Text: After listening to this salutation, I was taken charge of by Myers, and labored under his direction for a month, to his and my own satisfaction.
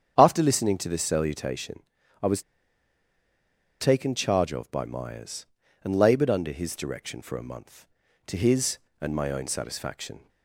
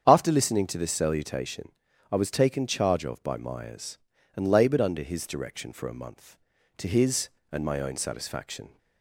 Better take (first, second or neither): second